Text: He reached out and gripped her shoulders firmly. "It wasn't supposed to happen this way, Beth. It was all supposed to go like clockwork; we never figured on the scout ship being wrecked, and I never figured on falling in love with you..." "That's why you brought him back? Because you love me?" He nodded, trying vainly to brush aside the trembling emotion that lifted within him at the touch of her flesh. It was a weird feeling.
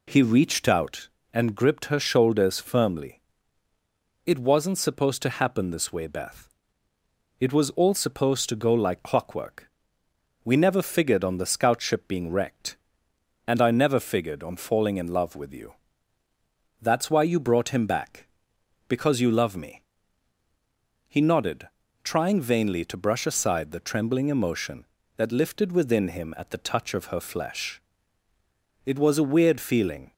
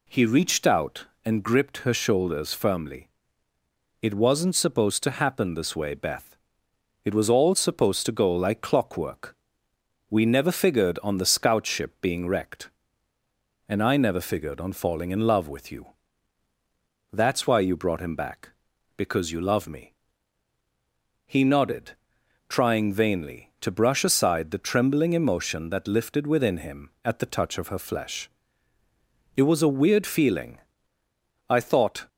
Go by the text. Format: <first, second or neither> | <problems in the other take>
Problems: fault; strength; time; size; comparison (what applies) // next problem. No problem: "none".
first | goes on to say "I thought"; from 31.4 s on; 0.60 s long